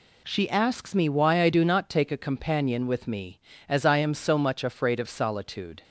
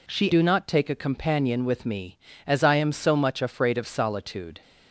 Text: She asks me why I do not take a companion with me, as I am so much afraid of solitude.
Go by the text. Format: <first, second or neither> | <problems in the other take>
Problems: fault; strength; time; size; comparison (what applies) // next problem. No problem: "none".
first | skips "asks me why I"; at 0.3 s